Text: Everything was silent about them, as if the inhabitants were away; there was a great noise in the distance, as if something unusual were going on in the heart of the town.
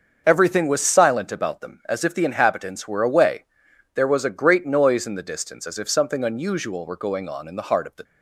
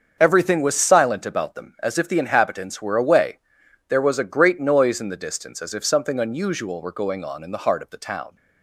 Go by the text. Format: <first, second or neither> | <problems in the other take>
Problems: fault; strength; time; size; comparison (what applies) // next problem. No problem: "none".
second | starts louder than the rest; until 1.2 s; 6.5 dB; also in the second // stops before "town"; at 8.0 s